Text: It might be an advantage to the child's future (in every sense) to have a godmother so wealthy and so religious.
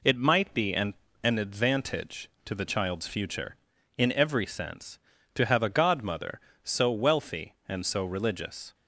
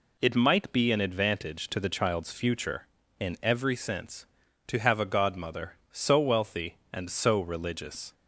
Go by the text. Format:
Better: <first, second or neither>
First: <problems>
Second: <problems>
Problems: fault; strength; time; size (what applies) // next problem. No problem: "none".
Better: second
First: says "an" twice; at 1.2 s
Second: none